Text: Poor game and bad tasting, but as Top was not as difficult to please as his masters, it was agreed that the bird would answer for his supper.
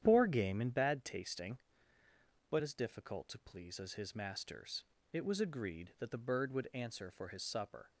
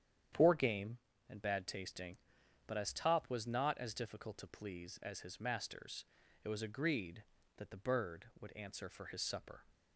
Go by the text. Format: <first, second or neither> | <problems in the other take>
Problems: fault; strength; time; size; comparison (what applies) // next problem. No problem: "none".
second | starts louder than the rest; strong; until 1.0 s; 9.5 dB; strong in the second // skips "as Top was not"; at 2.6 s